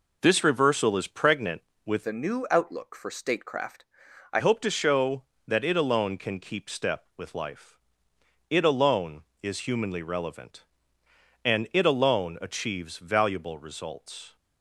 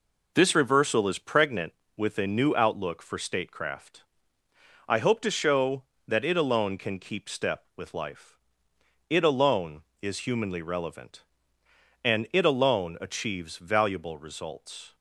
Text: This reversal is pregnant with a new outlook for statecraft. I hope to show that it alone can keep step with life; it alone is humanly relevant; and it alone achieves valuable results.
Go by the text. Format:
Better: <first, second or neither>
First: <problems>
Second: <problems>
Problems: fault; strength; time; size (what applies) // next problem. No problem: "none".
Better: second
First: changes voice from "a" to "I"; from 2.0 to 4.3 s; 2.3 s long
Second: none